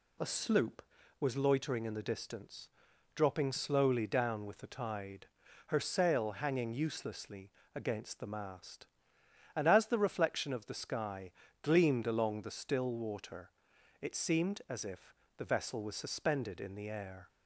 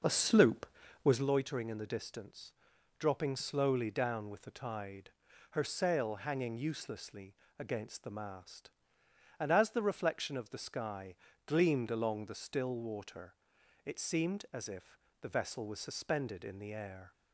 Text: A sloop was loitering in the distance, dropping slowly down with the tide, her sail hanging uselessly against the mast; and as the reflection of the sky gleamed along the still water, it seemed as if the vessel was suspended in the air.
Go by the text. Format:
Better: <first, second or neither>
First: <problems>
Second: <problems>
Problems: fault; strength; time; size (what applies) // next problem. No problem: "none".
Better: first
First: pauses between "uselessly" and "against"; slight; at 7.4 s; 0.26 s long // pauses between "sky" and "gleamed"; slight; at 11.2 s; 0.32 s long // pauses between "if" and "the"; slight; at 15.1 s; 0.22 s long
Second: starts louder than the rest; noticeable; until 1.3 s; 5.5 dB // pauses between "uselessly" and "against"; slight; at 7.3 s; 0.26 s long // pauses between "sky" and "gleamed"; slight; at 11.1 s; 0.32 s long // pauses between "if" and "the"; slight; at 14.9 s; 0.22 s long